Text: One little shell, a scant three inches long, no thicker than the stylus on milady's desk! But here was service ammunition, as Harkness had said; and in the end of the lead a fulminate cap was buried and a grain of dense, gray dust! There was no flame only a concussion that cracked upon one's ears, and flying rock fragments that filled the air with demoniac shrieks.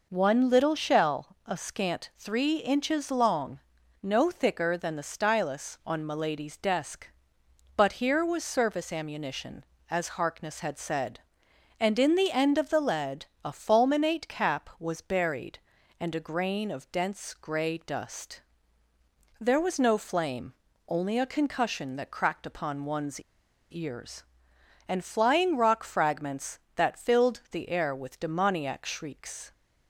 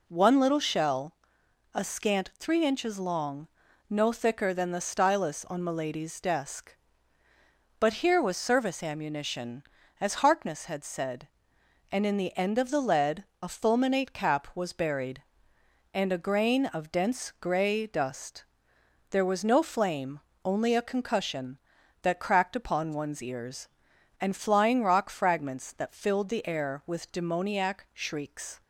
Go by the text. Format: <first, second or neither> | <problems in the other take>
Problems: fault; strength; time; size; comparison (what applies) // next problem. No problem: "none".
second | pauses between "lead" and "a"; slight; at 13.2 s; 0.18 s long; slight in the second // pauses between "flame" and "only"; slight; at 20.5 s; 0.32 s long; slight in the second // pauses between "one's" and "ears"; noticeable; at 23.2 s; 0.50 s long